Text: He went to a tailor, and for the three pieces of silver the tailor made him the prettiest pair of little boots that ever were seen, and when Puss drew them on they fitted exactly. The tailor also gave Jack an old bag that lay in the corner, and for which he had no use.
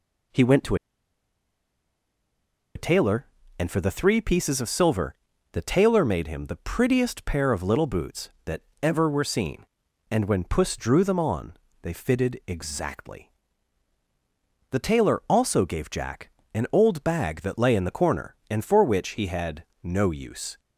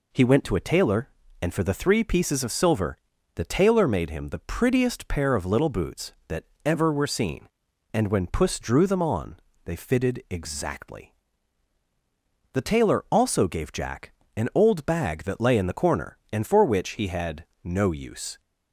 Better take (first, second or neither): second